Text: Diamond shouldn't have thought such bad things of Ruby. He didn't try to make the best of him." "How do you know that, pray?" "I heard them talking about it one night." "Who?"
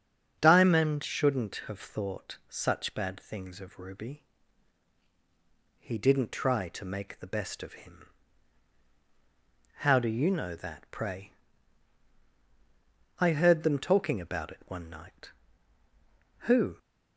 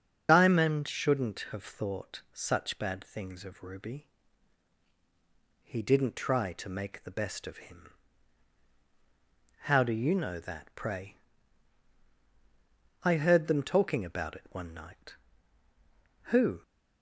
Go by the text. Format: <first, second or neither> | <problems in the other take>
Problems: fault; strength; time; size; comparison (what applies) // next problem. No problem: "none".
first | loses the start of "Diamond"; at 0.2 s; 55 ms // starts louder than the rest; until 1.3 s; 7 dB; strong in the first